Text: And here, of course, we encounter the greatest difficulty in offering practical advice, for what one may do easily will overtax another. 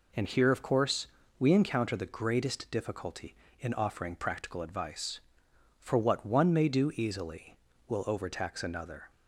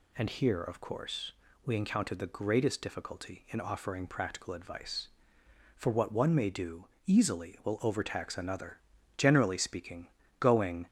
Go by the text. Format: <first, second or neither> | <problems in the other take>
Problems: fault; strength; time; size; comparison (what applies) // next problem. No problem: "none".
first | pauses between "do" and "easily"; slight; at 6.8 s; 0.20 s long // goes on to say "Generally speaking going"; strong; from 9.1 s on; 1.7 s long